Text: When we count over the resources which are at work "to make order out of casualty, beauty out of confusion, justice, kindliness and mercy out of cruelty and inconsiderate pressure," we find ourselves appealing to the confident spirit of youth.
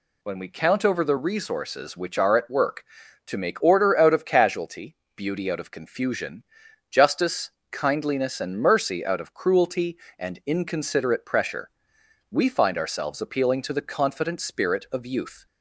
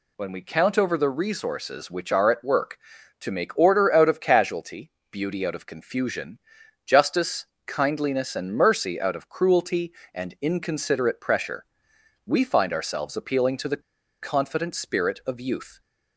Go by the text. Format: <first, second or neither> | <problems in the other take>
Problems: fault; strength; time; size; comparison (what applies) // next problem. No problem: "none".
first | pauses between "the" and "confident"; at 13.8 s; 0.39 s long